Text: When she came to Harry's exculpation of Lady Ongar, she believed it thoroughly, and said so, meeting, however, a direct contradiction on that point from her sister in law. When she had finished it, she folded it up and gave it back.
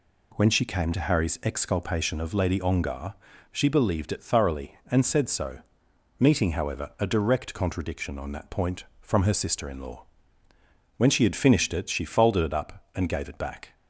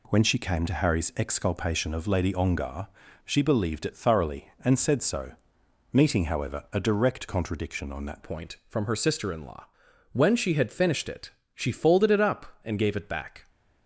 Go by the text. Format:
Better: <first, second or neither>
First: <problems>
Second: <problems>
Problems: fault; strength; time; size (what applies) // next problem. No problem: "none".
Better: first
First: none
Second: changes voice at "point"; from 8.2 s on; 5.2 s long